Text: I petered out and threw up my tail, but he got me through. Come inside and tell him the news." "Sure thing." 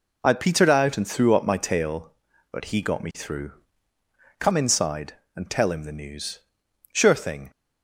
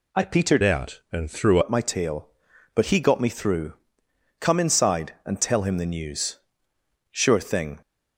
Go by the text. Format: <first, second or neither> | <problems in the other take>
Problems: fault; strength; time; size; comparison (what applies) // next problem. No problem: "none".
first | changes voice from "out" to "threw"; from 0.6 to 1.5 s; 0.9 s long